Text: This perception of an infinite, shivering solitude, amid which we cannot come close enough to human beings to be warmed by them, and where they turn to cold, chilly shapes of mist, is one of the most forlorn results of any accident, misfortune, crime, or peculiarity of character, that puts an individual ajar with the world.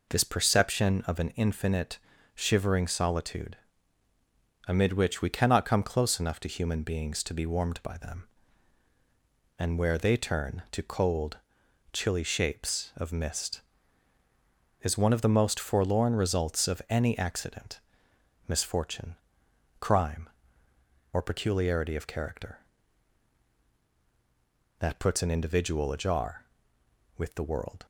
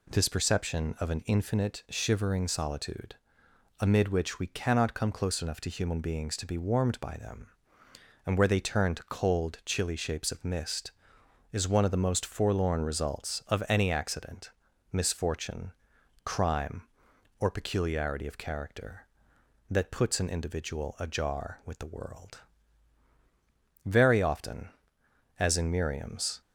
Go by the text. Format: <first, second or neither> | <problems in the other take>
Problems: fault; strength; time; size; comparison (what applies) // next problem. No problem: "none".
first | goes on to say "Very often as in Miriam's"; strong; from 23.8 s on; 2.5 s long